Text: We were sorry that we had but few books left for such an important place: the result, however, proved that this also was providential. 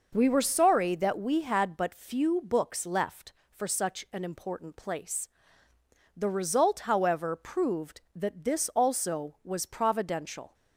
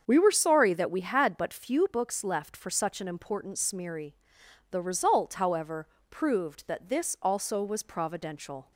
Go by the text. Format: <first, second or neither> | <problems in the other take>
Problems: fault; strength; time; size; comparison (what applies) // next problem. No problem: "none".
first | starts louder than the rest; until 1.0 s; 7 dB // says "smeary" for "place"; at 3.5 s